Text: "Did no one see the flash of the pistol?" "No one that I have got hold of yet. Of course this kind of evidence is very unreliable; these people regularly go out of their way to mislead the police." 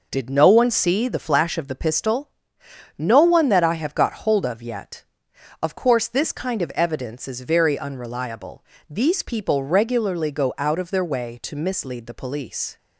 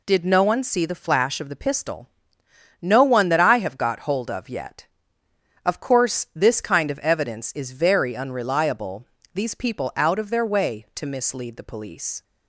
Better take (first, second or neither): first